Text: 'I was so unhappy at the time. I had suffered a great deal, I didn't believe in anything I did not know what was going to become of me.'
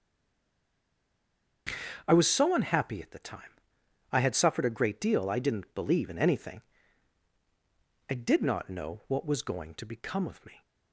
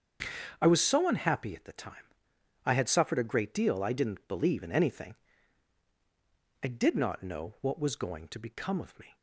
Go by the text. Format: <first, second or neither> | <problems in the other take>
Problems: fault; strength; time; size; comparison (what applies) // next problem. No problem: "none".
second | stays silent before the first word; noticeable; until 1.6 s; 1.6 s long // starts louder than the rest; until 3.0 s; 7 dB; also in the second // pauses between "anything" and "I"; strong; at 6.6 s; 1.4 s long; strong in the second